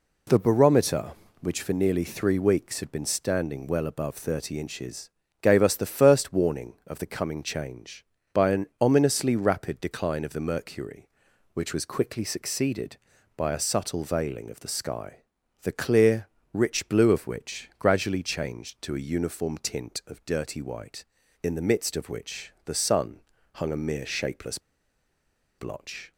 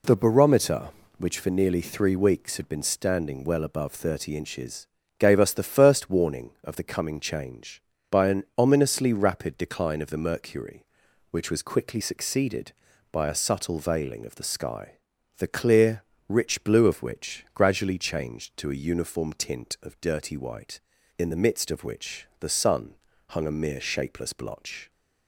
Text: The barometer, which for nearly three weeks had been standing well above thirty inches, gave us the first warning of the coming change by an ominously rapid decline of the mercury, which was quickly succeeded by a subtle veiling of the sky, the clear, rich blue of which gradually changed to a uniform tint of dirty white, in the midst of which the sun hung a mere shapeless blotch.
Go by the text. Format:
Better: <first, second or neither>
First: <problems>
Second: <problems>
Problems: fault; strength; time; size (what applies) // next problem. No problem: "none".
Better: second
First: pauses between "sun" and "hung"; slight; at 23.2 s; 0.34 s long // pauses between "shapeless" and "blotch"; at 24.5 s; 0.99 s long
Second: pauses between "sun" and "hung"; slight; at 22.9 s; 0.34 s long